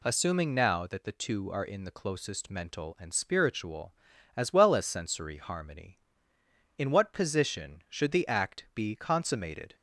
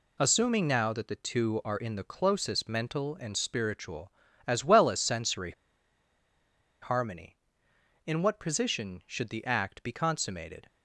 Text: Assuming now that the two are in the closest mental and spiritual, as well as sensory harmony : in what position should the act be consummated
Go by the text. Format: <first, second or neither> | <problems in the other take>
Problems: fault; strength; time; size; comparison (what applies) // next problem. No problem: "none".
first | pauses between "sensory" and "harmony"; strong; at 5.5 s; 1.3 s long